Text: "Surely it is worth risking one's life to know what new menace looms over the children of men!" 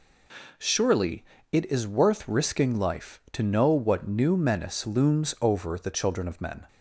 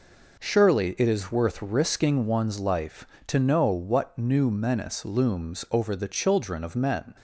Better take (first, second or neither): second